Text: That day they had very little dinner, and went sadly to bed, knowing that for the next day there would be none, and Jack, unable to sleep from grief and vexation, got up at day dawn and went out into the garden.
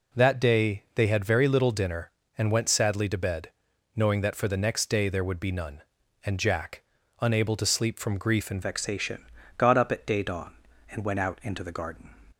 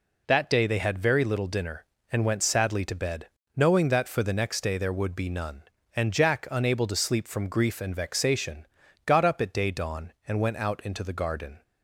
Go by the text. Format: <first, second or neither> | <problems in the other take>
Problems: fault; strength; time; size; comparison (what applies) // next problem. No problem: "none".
second | changes voice at "vexation"; from 8.6 s on; 3.4 s long